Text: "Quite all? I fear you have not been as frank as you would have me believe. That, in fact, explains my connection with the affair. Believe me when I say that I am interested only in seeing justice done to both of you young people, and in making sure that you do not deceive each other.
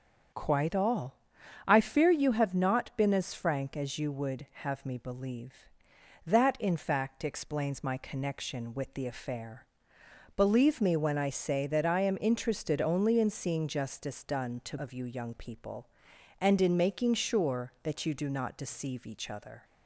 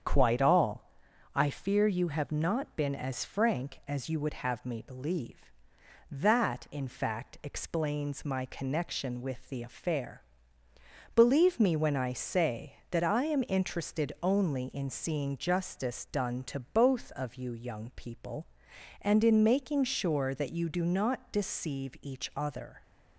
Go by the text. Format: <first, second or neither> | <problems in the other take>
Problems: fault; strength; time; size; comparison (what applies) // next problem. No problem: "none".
second | starts louder than the rest; strong; until 1.8 s; 7.5 dB; strong in the second // skips "both"; at 14.7 s